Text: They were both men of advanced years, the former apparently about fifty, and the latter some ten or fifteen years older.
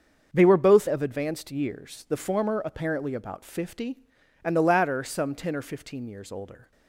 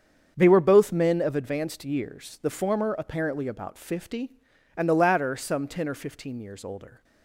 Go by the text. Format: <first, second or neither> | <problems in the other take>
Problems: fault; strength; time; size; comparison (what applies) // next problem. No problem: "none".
second | starts louder than the rest; until 1.3 s; 6.5 dB; strong in the second // skips "men"; at 0.8 s